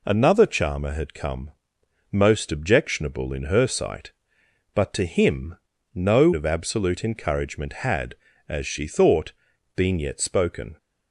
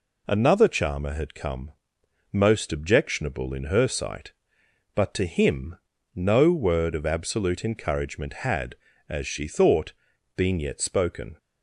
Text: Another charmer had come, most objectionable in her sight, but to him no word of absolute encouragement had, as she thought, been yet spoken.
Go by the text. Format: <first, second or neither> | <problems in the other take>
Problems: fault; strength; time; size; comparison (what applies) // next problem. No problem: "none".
second | pauses between "him" and "no"; at 5.5 s; 0.38 s long; also in the second // skips "word"; at 6.3 s